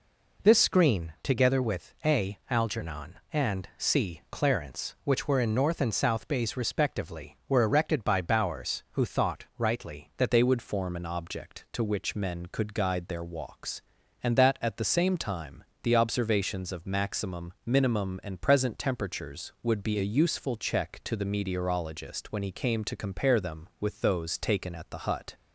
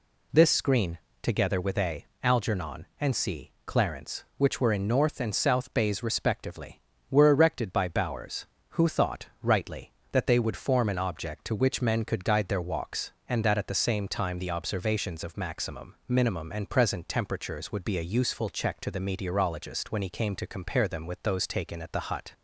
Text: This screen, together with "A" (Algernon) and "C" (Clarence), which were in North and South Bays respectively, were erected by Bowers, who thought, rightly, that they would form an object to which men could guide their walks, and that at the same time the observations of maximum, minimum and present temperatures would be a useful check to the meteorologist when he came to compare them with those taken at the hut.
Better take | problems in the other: second | changes voice at "they"; from 10.3 s on; 15.0 s long // pauses between "time" and "the"; slight; at 15.6 s; 0.18 s long

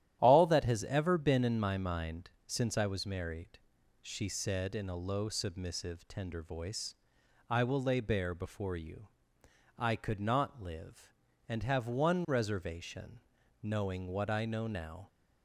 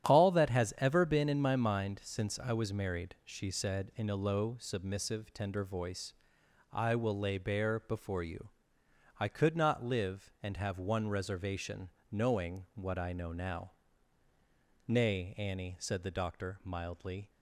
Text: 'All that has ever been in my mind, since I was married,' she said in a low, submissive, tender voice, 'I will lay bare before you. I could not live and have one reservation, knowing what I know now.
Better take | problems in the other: first | starts louder than the rest; strong; until 1.1 s; 10.5 dB; strong in the first // goes on to say "Nay Annie said the Doctor mildly"; strong; from 14.8 s on; 2.4 s long

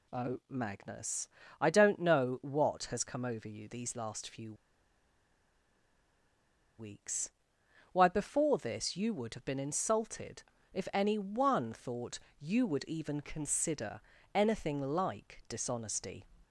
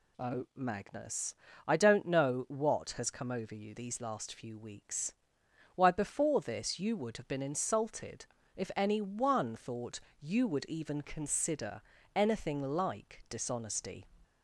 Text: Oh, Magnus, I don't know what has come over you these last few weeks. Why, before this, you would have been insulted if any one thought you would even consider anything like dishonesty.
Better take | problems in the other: second | pauses between "few" and "weeks"; strong; at 4.5 s; 2.2 s long // pauses between "insulted" and "if"; slight; at 10.4 s; 0.28 s long; slight in the second // pauses between "thought" and "you"; slight; at 12.2 s; 0.18 s long; slight in the second // pauses between "consider" and "anything"; slight; at 14.0 s; 0.32 s long; slight in the second

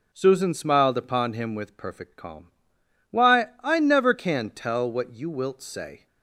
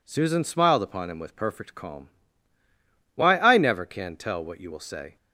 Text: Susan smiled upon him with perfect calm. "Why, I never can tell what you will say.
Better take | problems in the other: second | says "wilt" for "will"; at 5.3 s

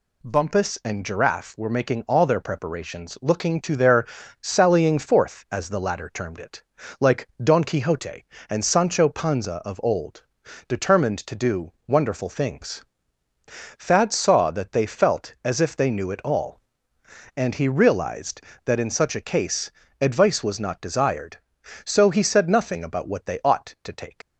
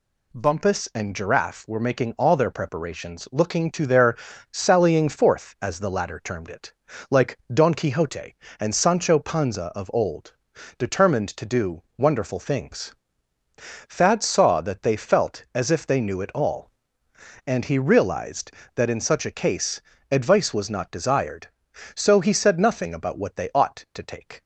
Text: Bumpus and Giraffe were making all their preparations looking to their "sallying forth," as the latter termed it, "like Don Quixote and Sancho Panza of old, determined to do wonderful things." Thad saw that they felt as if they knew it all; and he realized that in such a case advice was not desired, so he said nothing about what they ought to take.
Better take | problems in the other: second | pauses between "their" and "sallying"; slight; at 4.0 s; 0.34 s long; slight in the second // pauses between "like" and "Don"; slight; at 7.2 s; 0.16 s long; slight in the second // pauses between "do" and "wonderful"; slight; at 11.7 s; 0.16 s long; slight in the second // pauses between "case" and "advice"; slight; at 19.7 s; 0.30 s long; slight in the second // leaves "take" unfinished; at 24.2 s; 95 ms

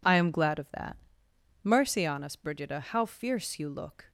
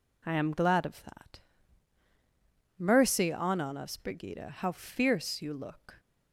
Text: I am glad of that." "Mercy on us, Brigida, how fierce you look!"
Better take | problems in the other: first | says "on" twice; at 3.5 s

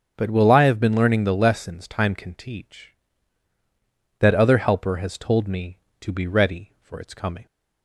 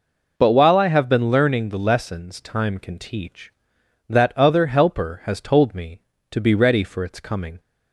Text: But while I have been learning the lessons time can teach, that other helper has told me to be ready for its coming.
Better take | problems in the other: second | starts louder than the rest; until 1.1 s; 6.5 dB // says "will" for "while"; at 0.2 s

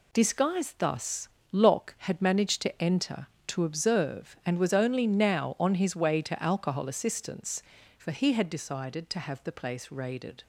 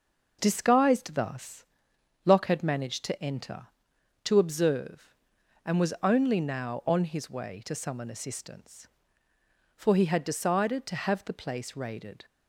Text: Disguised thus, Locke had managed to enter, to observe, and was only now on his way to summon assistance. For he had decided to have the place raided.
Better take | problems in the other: second | says "alcohol" for "summon"; at 6.4 s

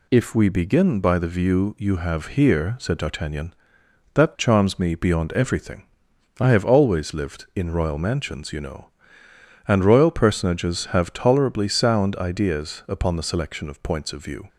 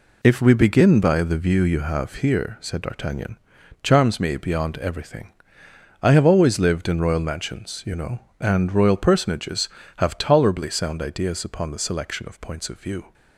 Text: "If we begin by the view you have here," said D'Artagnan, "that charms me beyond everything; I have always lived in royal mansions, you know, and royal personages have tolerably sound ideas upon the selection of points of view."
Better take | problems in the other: first | skips "that"; at 3.6 s

